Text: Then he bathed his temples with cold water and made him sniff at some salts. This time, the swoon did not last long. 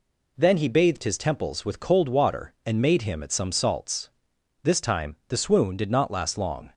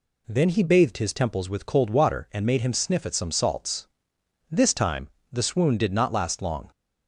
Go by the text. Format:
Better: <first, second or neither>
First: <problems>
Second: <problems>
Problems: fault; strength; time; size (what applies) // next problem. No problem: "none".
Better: second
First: skips "sniff"; at 3.2 s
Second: none